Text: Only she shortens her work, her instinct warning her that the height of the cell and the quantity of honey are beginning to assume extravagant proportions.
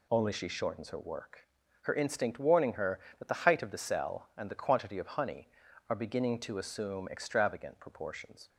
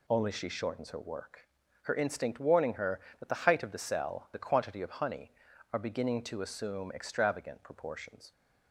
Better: first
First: none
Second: skips "and"; at 4.3 s

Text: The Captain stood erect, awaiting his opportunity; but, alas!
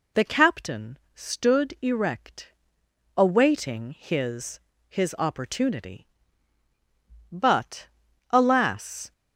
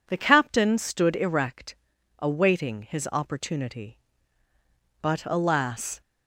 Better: second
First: pauses between "Captain" and "stood"; slight; at 0.9 s; 0.16 s long // says "his" twice; at 4.8 s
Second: none

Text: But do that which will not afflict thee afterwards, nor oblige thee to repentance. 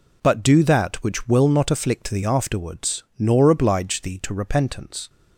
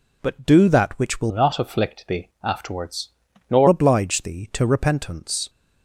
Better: first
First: none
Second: changes voice from "not" to "nor"; from 1.2 to 3.6 s; 2.4 s long

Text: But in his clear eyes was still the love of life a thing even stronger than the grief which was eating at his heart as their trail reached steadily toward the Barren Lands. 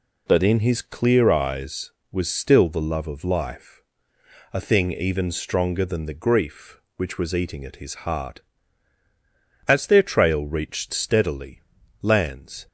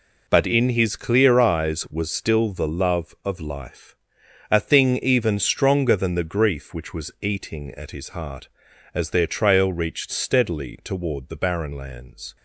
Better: second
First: pauses between "life" and "a"; noticeable; at 3.8 s; 0.70 s long // skips "toward the Barren"; at 11.8 s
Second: pauses between "life" and "a"; noticeable; at 3.9 s; 0.56 s long

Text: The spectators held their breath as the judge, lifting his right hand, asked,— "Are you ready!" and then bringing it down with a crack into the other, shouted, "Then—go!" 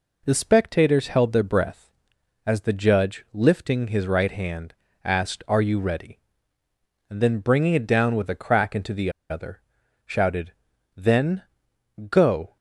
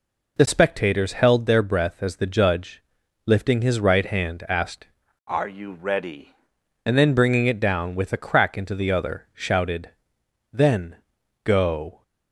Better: second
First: pauses between "the" and "other"; slight; at 9.1 s; 0.19 s long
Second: none

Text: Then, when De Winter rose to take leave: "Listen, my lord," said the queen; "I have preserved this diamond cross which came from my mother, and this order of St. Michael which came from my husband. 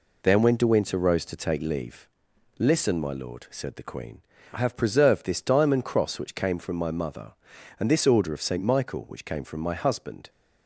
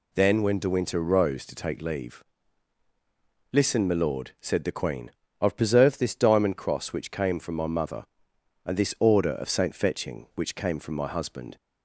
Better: first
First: none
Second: says "Fetching" for "Michael"; at 9.7 s

